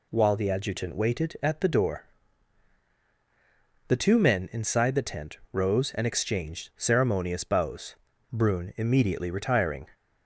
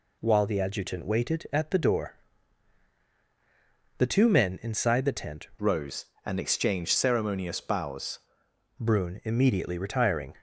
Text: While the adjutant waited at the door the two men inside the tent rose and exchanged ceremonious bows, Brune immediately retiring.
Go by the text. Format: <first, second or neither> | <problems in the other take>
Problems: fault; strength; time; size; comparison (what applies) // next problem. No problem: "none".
first | pauses between "door" and "the"; strong; at 2.1 s; 1.8 s long; strong in the first // changes voice from "rose" to "bows"; from 5.5 to 8.1 s; 2.6 s long